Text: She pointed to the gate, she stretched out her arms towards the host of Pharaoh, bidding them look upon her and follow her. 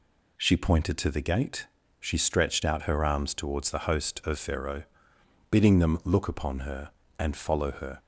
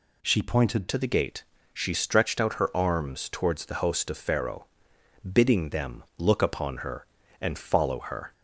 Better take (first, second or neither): first